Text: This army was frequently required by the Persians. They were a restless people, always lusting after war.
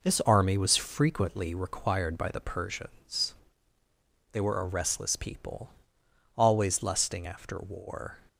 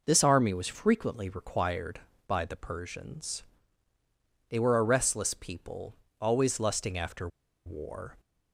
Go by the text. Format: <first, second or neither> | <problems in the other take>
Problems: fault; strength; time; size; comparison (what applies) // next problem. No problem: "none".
first | pauses between "after" and "war"; at 7.2 s; 0.38 s long